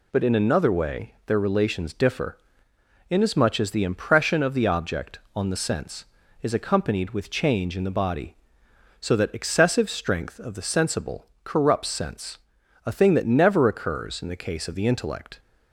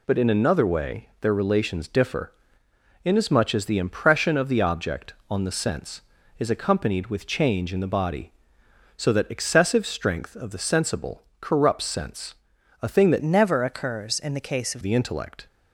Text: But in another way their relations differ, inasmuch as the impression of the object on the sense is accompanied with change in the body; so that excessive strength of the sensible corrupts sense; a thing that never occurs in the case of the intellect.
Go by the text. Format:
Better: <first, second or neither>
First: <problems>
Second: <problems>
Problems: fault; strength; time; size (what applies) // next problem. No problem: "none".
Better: first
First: pauses between "sensible" and "corrupts"; slight; at 11.2 s; 0.16 s long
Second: pauses between "sensible" and "corrupts"; slight; at 11.2 s; 0.16 s long // changes voice from "never" to "of"; from 13.2 to 14.8 s; 1.6 s long